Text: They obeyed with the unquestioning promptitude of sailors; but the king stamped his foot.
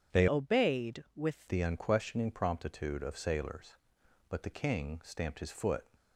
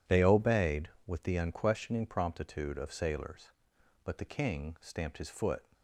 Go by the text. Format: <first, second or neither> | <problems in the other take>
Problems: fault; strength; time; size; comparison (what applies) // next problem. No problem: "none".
second | starts louder than the rest; strong; until 1.2 s; 7.5 dB // changes voice from "obeyed" to "with"; from 0.2 to 1.4 s; 1.2 s long